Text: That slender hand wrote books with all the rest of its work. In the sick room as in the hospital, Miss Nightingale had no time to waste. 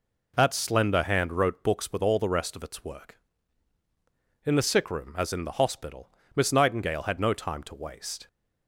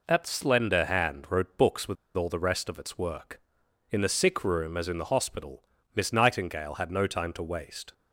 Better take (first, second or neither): first